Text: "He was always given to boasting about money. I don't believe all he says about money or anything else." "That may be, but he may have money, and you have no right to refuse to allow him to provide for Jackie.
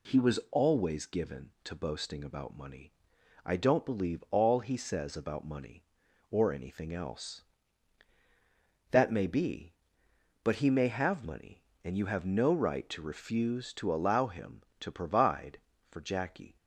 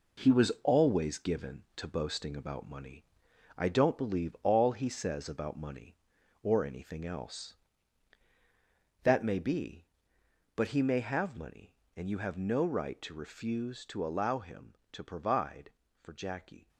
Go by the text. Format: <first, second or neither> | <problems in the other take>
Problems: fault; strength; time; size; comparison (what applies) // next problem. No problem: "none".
first | gets quieter; strong; throughout; 8 dB